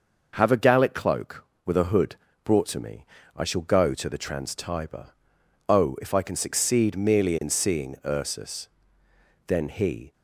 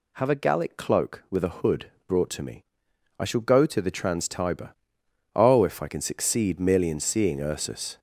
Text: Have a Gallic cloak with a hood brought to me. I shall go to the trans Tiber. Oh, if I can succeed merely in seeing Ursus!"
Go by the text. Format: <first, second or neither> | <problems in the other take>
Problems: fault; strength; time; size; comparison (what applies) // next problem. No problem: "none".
second | pauses between "hood" and "brought"; slight; at 2.1 s; 0.26 s long; slight in the second // goes on to say "Then he"; noticeable; from 9.4 s on; 0.66 s long